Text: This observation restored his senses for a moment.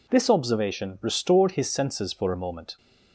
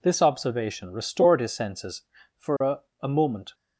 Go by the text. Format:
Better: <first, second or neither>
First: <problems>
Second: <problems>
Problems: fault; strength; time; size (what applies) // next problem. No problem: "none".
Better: first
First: none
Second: says "a" twice; at 3.0 s